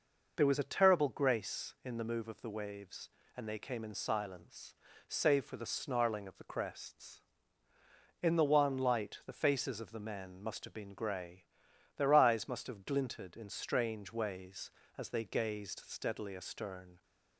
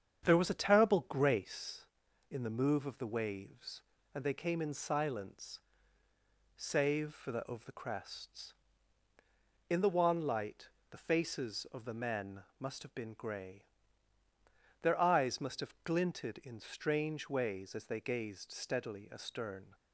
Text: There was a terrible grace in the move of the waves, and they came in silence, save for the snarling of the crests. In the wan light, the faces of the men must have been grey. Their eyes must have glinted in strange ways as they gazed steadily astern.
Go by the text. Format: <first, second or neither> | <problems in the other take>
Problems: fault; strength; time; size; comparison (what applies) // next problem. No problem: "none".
first | starts louder than the rest; strong; until 1.3 s; 8 dB // skips "snarling"; at 7.3 s